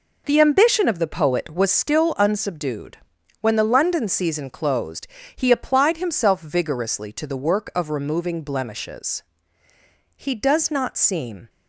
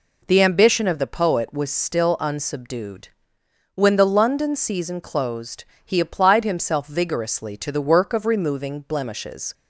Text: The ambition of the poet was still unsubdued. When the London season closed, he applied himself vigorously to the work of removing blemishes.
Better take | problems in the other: second | goes on to say "He does not seem"; from 10.1 s on; 1.3 s long

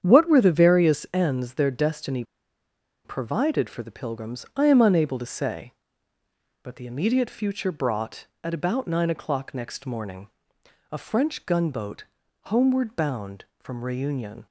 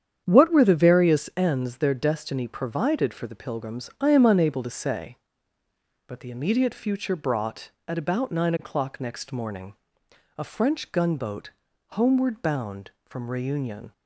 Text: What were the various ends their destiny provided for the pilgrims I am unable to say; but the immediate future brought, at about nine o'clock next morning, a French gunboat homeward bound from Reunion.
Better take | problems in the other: second | starts louder than the rest; strong; until 1.0 s; 8.5 dB; strong in the second // pauses between "destiny" and "provided"; noticeable; at 2.2 s; 0.81 s long // pauses between "gunboat" and "homeward"; at 12.0 s; 0.40 s long; also in the second

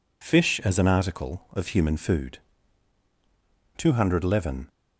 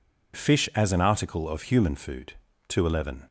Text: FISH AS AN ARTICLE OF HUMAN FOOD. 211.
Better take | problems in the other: neither | none

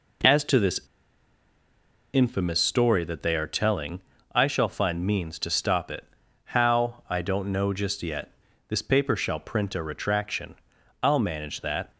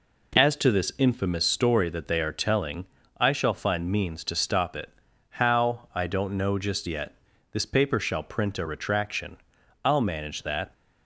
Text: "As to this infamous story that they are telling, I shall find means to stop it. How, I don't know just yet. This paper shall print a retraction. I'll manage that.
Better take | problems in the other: second | pauses between "this" and "infamous"; strong; at 0.7 s; 1.3 s long

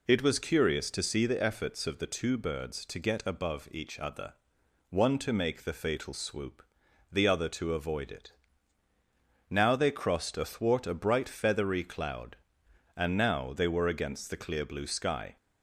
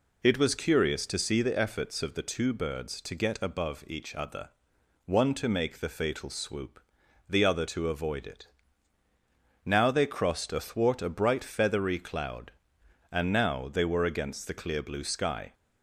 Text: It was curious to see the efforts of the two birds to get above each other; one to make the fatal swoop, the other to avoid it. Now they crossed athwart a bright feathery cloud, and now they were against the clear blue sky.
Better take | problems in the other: neither | none

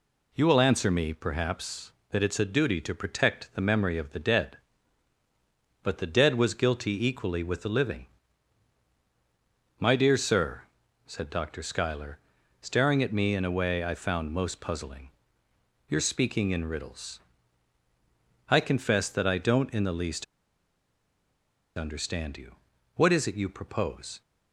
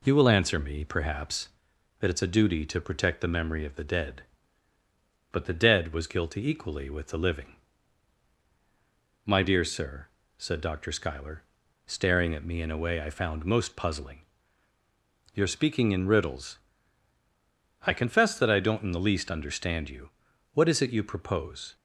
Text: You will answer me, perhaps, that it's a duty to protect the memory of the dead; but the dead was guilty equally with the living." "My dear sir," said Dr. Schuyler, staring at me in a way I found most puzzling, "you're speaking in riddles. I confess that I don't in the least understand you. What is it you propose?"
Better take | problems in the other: second | pauses between "least" and "understand"; strong; at 20.2 s; 1.5 s long

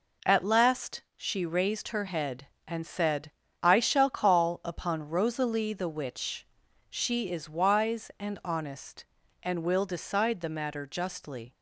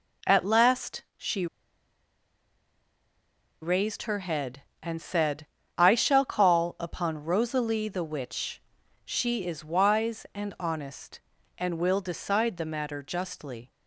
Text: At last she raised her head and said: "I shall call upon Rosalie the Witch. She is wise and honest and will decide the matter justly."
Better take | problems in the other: first | pauses between "she" and "raised"; strong; at 1.4 s; 2.1 s long

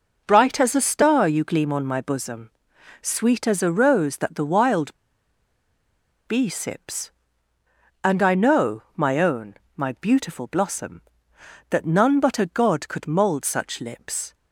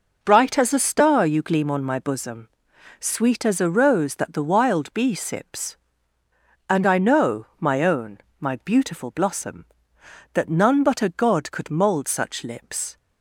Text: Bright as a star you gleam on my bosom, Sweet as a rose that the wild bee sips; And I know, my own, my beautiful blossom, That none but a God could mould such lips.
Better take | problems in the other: second | pauses between "wild" and "bee"; strong; at 4.9 s; 1.3 s long

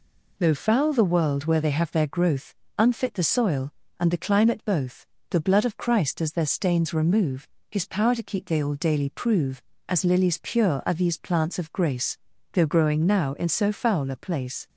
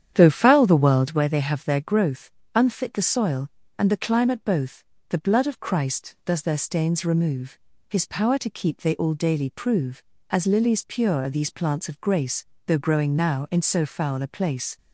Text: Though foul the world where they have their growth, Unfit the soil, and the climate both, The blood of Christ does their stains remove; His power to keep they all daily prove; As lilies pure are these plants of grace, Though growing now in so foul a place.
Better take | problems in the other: first | starts louder than the rest; strong; until 1.2 s; 9.5 dB

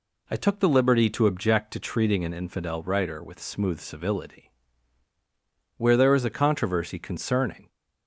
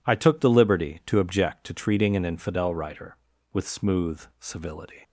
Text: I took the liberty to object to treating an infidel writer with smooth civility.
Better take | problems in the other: second | goes on to say "Where there is a controversy concerning"; strong; from 5.7 s on; 1.9 s long

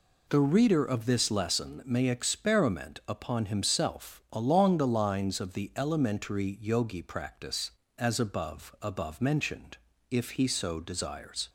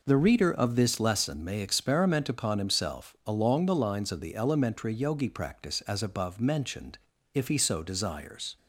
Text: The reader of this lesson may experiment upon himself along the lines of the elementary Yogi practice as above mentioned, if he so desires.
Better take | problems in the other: second | says "above" twice; at 8.8 s

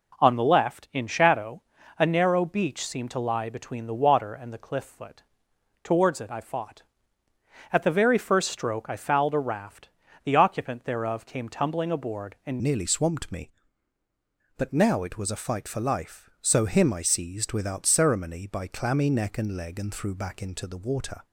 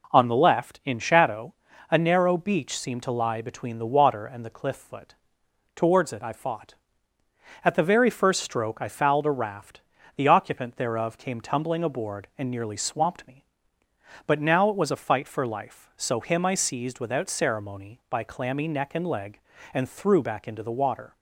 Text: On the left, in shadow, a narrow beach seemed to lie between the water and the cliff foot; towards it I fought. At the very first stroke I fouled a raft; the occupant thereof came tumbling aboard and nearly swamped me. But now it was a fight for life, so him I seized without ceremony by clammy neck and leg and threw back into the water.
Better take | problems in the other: second | changes voice at "nearly"; from 12.6 s on; 8.6 s long

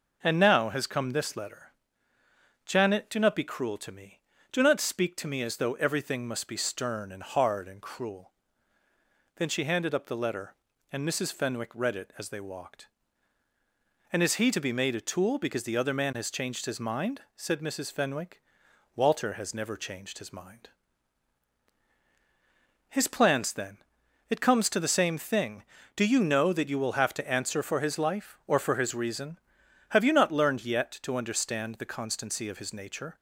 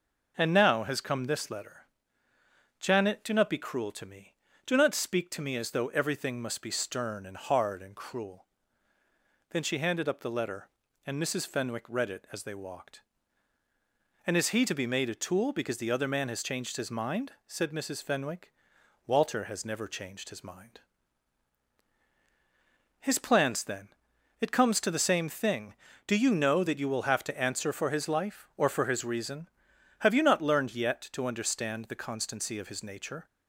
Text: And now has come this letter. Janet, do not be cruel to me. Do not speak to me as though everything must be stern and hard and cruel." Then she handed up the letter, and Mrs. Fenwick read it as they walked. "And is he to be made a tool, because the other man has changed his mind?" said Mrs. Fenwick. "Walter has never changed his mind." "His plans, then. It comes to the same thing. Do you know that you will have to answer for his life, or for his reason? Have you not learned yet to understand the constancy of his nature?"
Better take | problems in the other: neither | none

